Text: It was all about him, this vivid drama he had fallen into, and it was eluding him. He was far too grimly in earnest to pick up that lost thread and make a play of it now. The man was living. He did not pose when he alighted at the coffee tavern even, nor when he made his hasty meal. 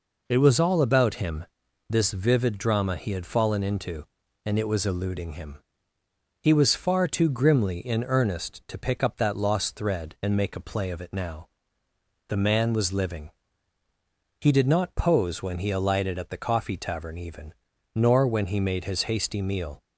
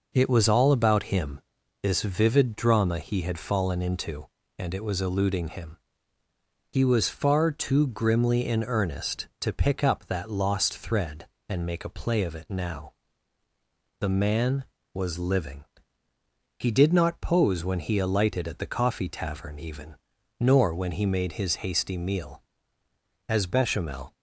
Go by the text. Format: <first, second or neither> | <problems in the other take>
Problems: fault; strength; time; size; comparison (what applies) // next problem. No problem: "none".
first | goes on to say "As Bechamel"; noticeable; from 23.2 s on; 0.86 s long